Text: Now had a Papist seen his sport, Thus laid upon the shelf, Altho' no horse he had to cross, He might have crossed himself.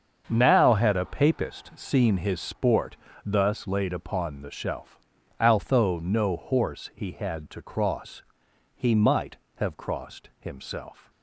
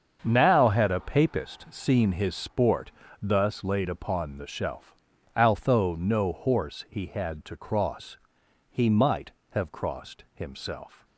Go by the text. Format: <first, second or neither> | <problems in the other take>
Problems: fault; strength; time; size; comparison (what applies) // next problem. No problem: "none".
neither | starts louder than the rest; the same in both